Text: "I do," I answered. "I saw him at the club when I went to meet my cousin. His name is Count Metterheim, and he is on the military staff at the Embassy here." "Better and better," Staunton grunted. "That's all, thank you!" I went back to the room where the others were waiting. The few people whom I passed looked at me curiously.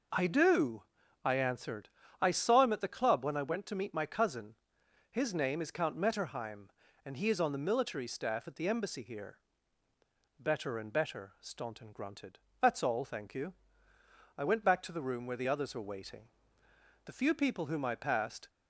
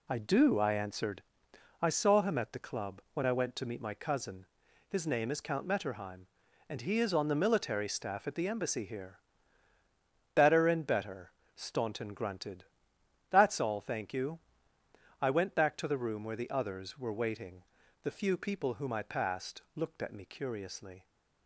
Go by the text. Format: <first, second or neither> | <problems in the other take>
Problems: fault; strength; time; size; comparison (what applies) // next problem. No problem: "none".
second | stops before "looked at me curiously"; at 18.4 s